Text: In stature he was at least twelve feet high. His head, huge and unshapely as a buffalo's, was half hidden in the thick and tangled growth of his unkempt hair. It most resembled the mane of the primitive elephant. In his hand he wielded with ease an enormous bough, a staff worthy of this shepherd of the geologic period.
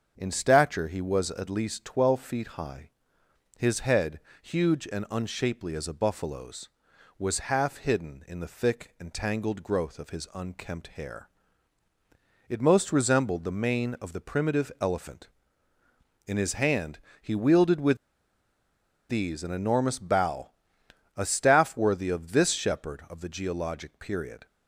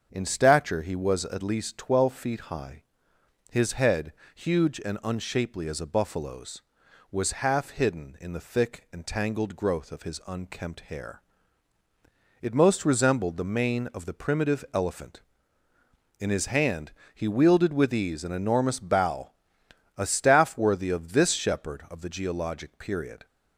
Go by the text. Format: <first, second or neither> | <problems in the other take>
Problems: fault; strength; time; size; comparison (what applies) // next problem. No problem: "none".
second | starts louder than the rest; until 1.1 s; 7 dB; also in the second // pauses between "hand" and "he"; slight; at 16.9 s; 0.22 s long; slight in the second // pauses between "with" and "ease"; at 17.9 s; 1.1 s long